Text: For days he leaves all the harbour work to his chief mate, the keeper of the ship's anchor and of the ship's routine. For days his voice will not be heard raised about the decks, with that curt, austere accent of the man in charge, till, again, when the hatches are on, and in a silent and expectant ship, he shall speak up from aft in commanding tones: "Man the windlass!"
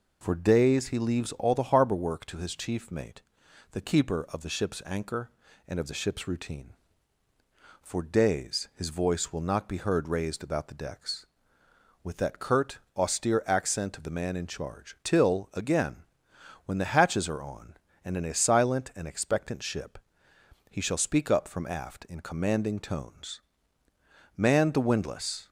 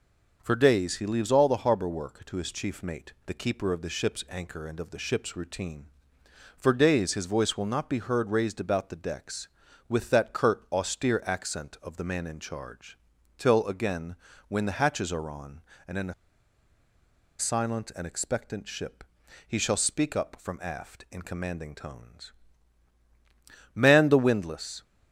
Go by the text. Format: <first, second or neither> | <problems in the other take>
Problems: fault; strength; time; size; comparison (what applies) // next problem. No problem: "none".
first | pauses between "a" and "silent"; strong; at 16.1 s; 1.2 s long